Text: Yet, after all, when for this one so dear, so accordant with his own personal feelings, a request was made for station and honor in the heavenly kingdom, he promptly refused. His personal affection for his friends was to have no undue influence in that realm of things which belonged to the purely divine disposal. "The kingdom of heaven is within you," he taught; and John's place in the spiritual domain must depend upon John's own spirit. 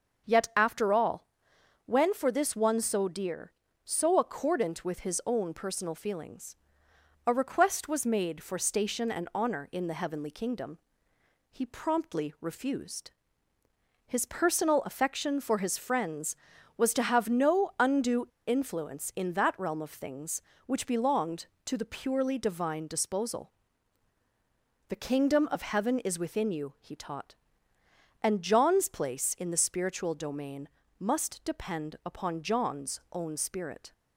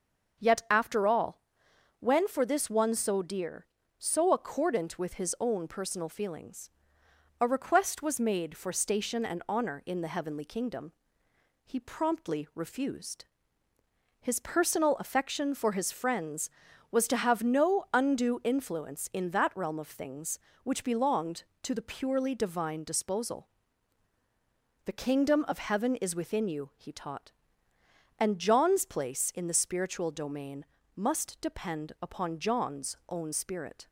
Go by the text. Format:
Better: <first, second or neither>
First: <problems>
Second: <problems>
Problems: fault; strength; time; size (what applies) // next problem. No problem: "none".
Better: second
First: starts louder than the rest; until 1.9 s; 6 dB // pauses between "undue" and "influence"; slight; at 18.2 s; 0.21 s long // pauses between "domain" and "must"; slight; at 30.6 s; 0.30 s long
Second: starts louder than the rest; until 2.0 s; 6 dB // pauses between "domain" and "must"; slight; at 30.6 s; 0.30 s long